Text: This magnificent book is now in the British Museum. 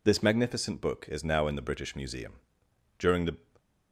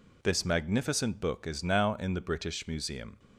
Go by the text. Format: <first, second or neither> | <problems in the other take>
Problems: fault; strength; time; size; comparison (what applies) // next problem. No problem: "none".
second | goes on to say "During the"; slight; from 2.9 s on; 0.38 s long